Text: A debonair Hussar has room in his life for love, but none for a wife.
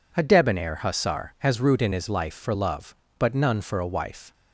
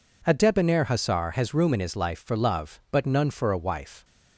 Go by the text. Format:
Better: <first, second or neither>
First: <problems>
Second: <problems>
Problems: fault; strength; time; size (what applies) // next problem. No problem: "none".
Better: second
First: says "root" for "room"; at 1.5 s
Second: none